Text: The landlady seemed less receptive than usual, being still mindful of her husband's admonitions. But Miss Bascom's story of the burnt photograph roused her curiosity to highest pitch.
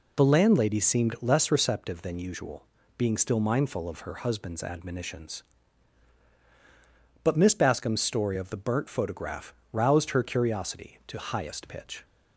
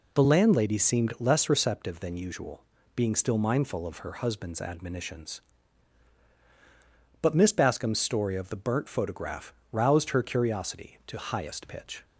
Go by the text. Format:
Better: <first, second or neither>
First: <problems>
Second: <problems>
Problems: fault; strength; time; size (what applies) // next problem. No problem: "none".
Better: neither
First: pauses between "photograph" and "roused"; slight; at 9.5 s; 0.18 s long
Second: pauses between "photograph" and "roused"; slight; at 9.5 s; 0.18 s long